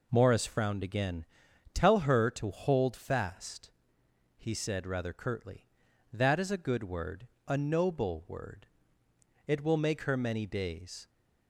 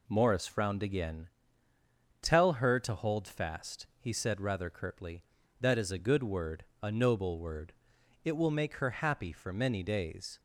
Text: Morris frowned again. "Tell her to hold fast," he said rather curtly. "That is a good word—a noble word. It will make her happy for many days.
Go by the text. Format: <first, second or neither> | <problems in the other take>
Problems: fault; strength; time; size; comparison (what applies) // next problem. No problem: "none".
second | skips "happy for"; at 10.1 s